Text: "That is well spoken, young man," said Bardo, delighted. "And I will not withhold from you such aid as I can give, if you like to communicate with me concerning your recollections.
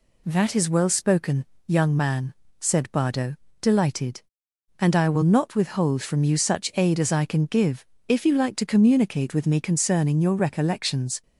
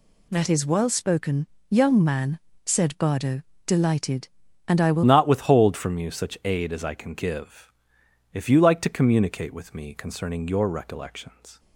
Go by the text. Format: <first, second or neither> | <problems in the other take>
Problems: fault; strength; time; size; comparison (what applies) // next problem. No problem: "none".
first | changes voice at "not"; from 5.0 s on; 6.5 s long